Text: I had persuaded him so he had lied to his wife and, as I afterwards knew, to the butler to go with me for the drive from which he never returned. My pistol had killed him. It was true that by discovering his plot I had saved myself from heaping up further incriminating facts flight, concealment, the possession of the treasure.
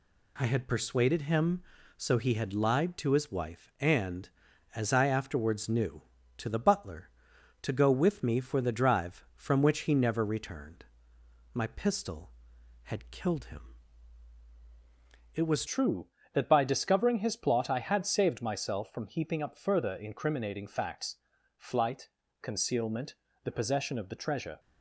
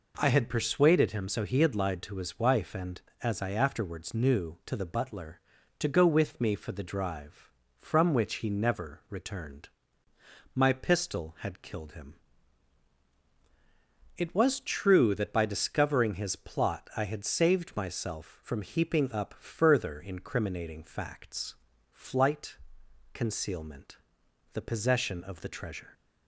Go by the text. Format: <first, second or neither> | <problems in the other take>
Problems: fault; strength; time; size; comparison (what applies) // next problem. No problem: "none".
second | changes voice at "true"; from 15.6 s on; 8.9 s long // pauses between "facts" and "flight"; at 21.1 s; 0.42 s long; slight in the second